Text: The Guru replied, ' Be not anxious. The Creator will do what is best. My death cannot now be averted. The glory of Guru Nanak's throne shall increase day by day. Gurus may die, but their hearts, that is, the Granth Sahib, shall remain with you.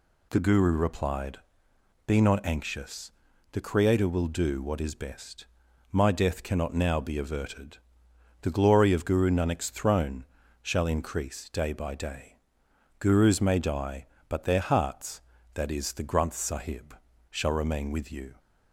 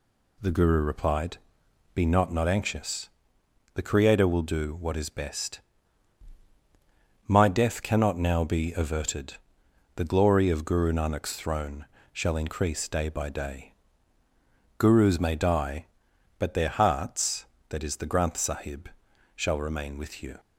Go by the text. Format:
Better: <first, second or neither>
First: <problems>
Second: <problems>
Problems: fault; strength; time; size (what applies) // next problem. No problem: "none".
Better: first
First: pauses between "throne" and "shall"; slight; at 10.2 s; 0.36 s long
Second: says "not" twice; at 2.3 s // pauses between "throne" and "shall"; slight; at 11.8 s; 0.26 s long